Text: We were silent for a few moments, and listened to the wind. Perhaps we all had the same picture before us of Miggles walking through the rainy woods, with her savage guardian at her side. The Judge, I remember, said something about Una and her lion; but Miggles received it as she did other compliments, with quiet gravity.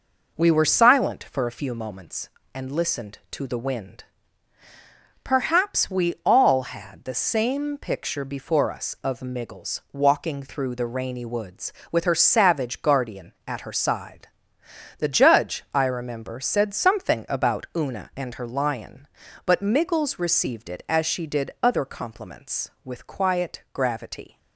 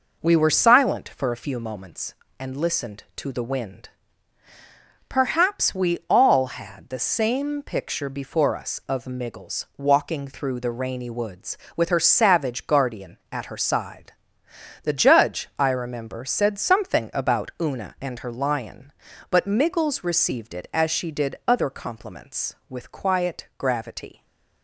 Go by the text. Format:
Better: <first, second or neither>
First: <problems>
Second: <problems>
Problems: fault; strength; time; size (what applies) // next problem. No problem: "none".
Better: neither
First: none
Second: none